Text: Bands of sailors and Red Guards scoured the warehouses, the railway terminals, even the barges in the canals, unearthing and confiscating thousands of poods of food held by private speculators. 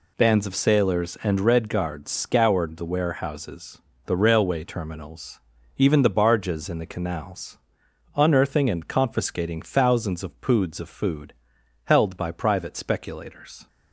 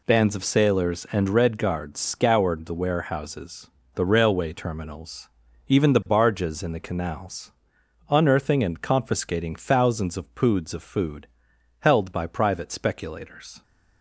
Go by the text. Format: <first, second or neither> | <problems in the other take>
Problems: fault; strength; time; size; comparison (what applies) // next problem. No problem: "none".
neither | pauses between "food" and "held"; noticeable; the same in both